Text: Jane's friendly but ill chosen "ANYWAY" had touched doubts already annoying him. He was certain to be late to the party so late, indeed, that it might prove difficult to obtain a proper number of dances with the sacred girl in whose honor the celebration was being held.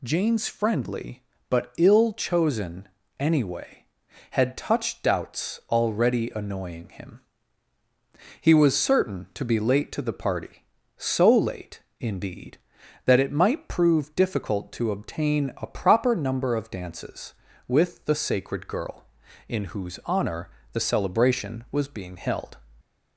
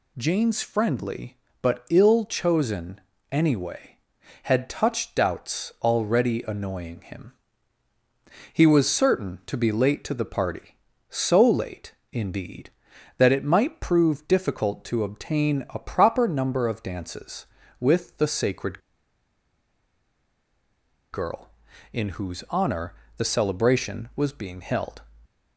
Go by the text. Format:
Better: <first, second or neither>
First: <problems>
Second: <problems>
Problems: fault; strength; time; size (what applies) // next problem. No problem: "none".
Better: first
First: pauses between "chosen" and "ANYWAY"; slight; at 2.8 s; 0.32 s long // pauses between "honor" and "the"; slight; at 20.4 s; 0.24 s long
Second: pauses between "chosen" and "ANYWAY"; slight; at 2.9 s; 0.32 s long // pauses between "sacred" and "girl"; strong; at 18.7 s; 2.3 s long // pauses between "honor" and "the"; slight; at 22.9 s; 0.24 s long